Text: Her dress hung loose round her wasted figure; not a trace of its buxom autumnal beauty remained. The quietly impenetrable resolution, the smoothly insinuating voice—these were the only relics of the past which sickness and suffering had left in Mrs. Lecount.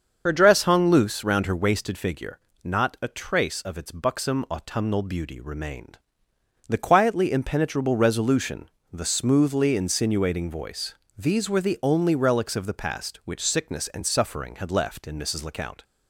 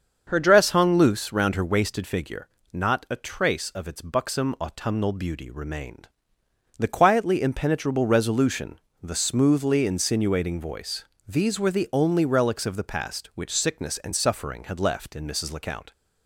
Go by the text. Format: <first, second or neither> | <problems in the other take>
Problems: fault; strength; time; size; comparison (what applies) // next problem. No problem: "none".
second | loses the start of "Her"; at 0.2 s; 55 ms // starts louder than the rest; until 1.2 s; 6.5 dB; also in the second